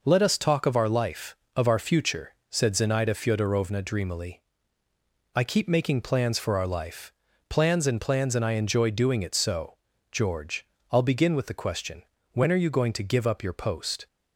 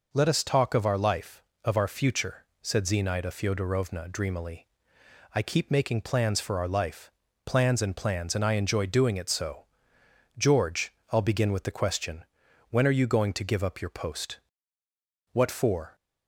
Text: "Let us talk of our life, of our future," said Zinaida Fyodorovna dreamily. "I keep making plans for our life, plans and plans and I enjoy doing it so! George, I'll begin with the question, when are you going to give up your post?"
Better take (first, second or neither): first